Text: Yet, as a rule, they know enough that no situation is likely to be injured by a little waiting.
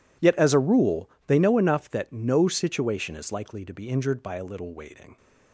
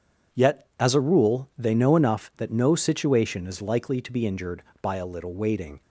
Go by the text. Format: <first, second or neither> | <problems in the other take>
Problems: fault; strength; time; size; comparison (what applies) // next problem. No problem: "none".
second | gets quieter; strong; throughout; 18.5 dB